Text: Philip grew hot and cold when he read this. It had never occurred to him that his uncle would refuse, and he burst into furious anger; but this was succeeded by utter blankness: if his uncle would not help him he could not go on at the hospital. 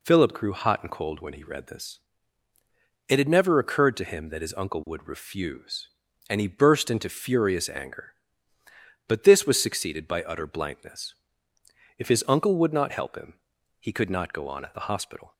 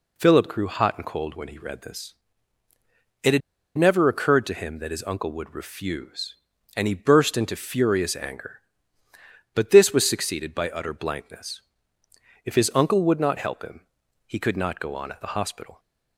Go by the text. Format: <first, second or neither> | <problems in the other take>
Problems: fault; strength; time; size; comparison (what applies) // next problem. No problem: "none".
first | pauses between "had" and "never"; at 3.4 s; 0.37 s long // pauses between "him" and "he"; at 13.8 s; 0.40 s long; also in the first